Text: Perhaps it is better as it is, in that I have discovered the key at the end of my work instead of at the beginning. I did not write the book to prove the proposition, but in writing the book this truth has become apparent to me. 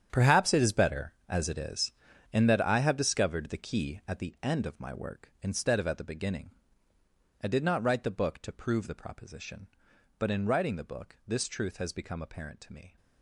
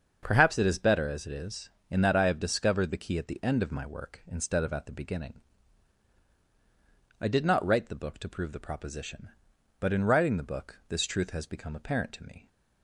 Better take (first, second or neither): second